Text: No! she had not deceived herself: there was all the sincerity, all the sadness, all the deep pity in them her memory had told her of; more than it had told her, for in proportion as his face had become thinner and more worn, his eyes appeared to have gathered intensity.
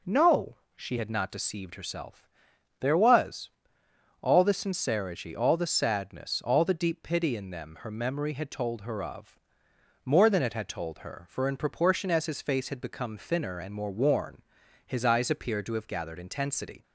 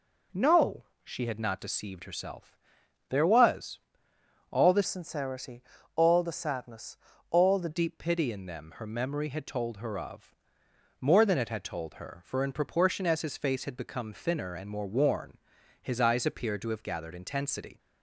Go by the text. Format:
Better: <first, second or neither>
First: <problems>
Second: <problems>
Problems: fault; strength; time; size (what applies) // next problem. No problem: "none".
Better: first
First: pauses between "was" and "all"; noticeable; at 3.5 s; 0.72 s long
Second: pauses between "was" and "all"; noticeable; at 3.8 s; 0.72 s long // changes voice from "sincerity" to "the"; from 4.8 to 7.6 s; 2.8 s long